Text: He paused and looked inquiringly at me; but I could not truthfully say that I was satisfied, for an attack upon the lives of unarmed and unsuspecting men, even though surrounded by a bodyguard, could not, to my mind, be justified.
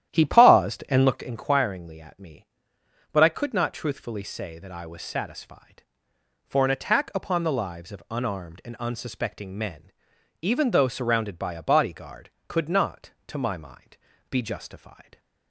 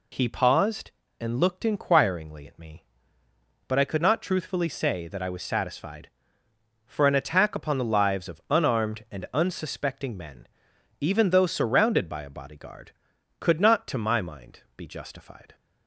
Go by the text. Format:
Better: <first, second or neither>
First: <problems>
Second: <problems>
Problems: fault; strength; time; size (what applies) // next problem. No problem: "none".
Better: second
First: starts louder than the rest; strong; until 1.3 s; 11.5 dB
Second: none